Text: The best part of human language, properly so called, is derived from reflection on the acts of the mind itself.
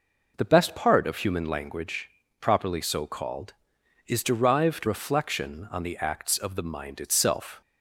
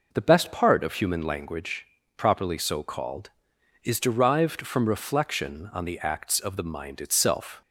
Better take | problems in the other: second | skips "from"; at 4.8 s

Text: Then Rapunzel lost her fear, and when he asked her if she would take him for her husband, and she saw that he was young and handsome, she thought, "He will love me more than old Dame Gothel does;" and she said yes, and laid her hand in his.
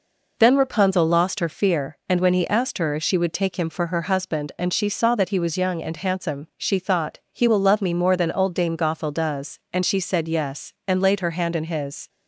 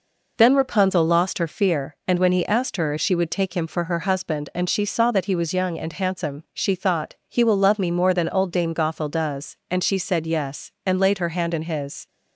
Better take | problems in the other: neither | none

